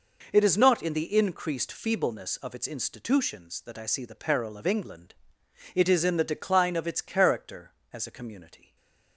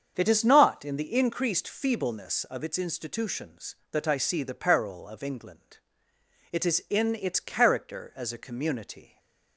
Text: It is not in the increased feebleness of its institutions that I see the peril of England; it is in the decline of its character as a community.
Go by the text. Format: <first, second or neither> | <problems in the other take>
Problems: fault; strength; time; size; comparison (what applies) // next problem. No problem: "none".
first | starts louder than the rest; strong; until 1.1 s; 7 dB // skips "the decline of"; at 7.1 s // stays silent after the last word; slight; from 9.0 s on; 0.5 s long; slight in the first